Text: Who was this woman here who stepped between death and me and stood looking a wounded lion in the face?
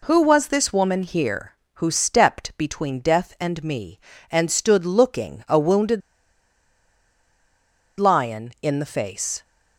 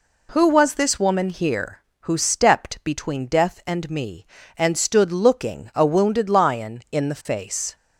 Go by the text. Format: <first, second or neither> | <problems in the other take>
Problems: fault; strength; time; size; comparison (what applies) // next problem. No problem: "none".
second | pauses between "wounded" and "lion"; strong; at 6.0 s; 1.9 s long